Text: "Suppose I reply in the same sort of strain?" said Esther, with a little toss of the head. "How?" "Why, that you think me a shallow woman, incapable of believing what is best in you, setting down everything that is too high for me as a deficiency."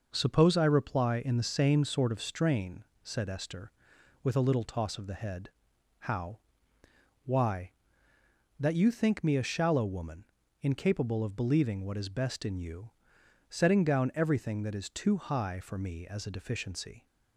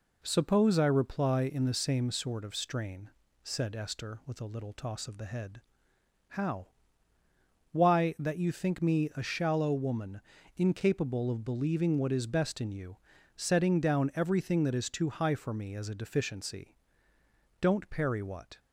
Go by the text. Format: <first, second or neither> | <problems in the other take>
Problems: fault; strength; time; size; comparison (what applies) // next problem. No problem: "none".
first | goes on to say "Don't parry what"; noticeable; from 17.5 s on; 1.0 s long